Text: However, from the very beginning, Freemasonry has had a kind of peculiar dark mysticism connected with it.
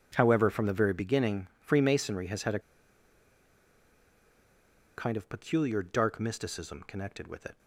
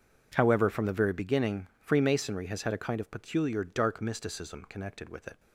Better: second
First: pauses between "a" and "kind"; strong; at 2.5 s; 2.3 s long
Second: none

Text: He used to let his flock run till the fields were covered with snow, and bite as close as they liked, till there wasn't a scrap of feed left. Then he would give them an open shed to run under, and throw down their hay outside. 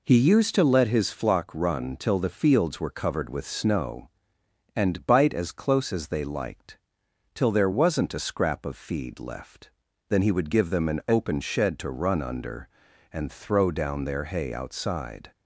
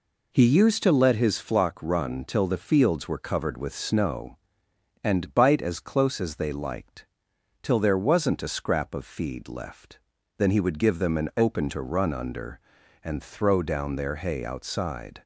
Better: first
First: none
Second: skips "shed"; at 11.6 s

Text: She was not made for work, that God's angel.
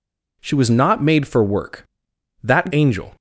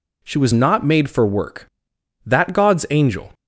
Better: second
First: skips "God's"; at 2.7 s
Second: none

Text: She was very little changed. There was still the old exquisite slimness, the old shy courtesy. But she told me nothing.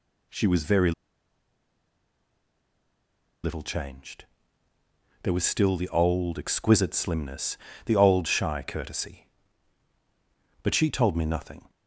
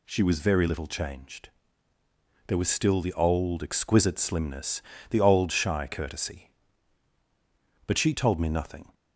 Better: second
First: pauses between "very" and "little"; strong; at 0.9 s; 2.5 s long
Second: none

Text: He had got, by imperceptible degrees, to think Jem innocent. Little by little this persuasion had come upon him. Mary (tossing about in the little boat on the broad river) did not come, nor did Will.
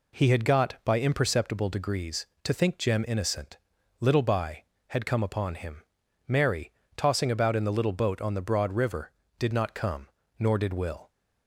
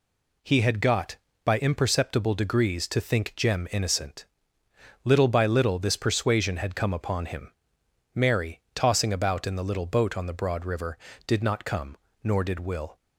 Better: second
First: skips "little this persuasion"; at 4.7 s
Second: none

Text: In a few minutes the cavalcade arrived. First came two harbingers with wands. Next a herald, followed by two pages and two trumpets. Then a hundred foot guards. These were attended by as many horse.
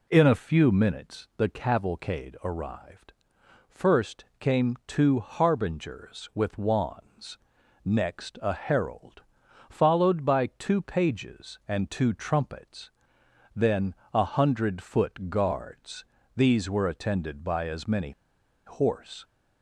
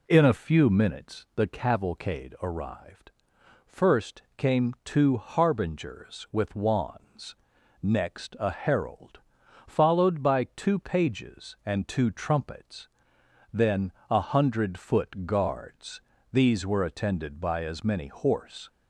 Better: second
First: pauses between "First" and "came"; slight; at 4.2 s; 0.16 s long // pauses between "Then" and "a"; slight; at 13.9 s; 0.20 s long // pauses between "many" and "horse"; noticeable; at 18.1 s; 0.54 s long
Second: pauses between "First" and "came"; slight; at 4.2 s; 0.16 s long // pauses between "Then" and "a"; slight; at 13.9 s; 0.18 s long

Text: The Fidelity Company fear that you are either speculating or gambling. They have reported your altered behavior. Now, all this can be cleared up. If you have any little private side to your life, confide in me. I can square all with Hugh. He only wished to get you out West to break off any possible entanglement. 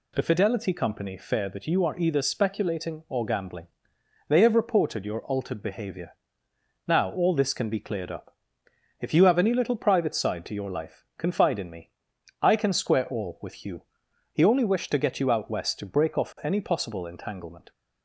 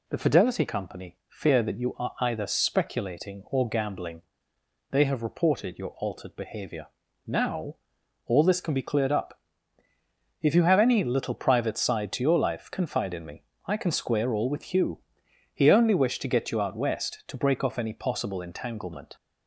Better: neither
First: none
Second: none

